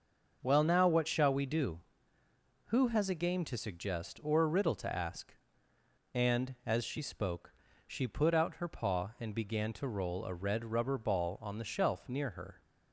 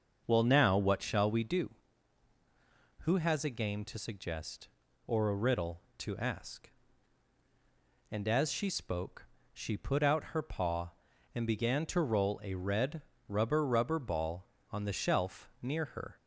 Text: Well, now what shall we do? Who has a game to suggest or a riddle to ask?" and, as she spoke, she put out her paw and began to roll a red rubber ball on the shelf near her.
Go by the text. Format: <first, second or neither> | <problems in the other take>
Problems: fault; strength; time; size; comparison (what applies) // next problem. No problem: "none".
first | starts louder than the rest; until 1.2 s; 6 dB; noticeable in the first // pauses between "red" and "rubber"; slight; at 13.0 s; 0.26 s long // says "rubber" twice; at 13.6 s